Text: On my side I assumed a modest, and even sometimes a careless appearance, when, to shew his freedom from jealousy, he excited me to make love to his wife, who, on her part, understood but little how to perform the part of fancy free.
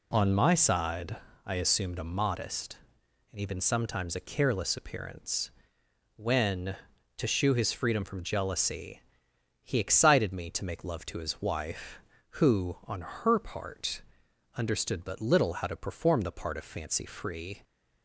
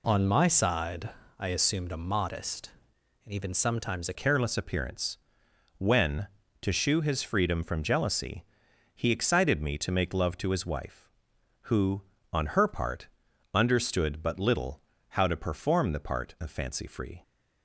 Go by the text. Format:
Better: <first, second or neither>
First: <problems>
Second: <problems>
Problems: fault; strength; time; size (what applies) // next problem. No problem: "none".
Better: first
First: pauses between "side" and "I"; slight; at 1.1 s; 0.30 s long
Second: pauses between "side" and "I"; slight; at 1.0 s; 0.30 s long // changes voice at "careless"; from 4.1 s on; 13.1 s long // pauses between "little" and "how"; slight; at 14.8 s; 0.30 s long